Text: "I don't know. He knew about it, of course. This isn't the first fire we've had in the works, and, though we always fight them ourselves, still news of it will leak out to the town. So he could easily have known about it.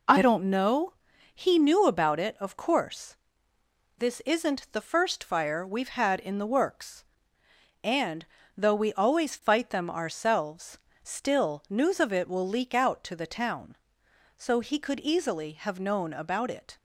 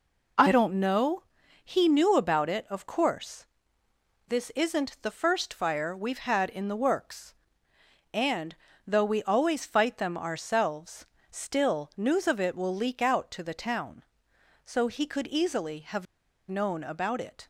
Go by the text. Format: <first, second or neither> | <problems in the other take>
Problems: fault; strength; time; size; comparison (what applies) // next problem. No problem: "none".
first | pauses between "have" and "known"; at 16.0 s; 0.43 s long